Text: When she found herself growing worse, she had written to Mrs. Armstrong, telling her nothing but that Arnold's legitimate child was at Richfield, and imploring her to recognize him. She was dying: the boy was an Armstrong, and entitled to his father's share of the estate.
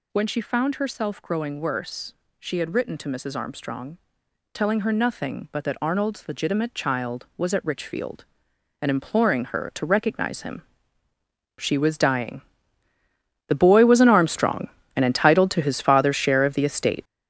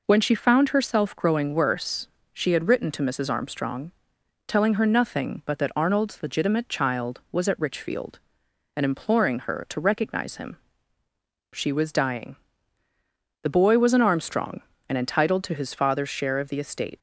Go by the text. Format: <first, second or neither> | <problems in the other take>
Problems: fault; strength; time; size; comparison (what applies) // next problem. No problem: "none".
second | gets louder; strong; throughout; 9.5 dB